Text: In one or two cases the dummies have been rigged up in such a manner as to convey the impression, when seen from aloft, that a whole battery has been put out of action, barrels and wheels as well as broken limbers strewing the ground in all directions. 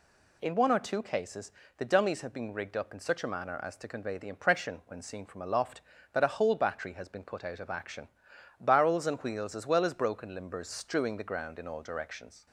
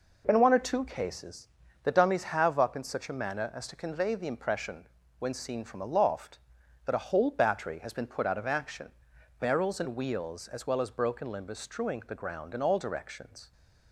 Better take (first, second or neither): first